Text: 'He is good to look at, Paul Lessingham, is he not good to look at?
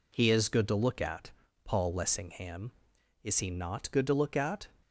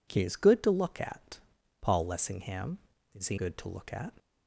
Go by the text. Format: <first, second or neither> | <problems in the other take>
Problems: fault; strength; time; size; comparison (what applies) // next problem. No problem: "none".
first | skips "not"; at 3.3 s